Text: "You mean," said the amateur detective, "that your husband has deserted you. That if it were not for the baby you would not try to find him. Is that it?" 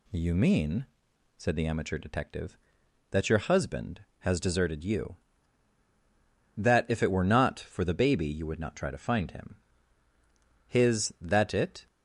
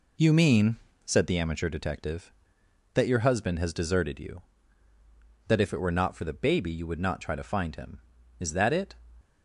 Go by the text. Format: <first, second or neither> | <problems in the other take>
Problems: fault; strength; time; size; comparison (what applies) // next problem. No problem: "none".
second | says "His" for "Is"; at 10.6 s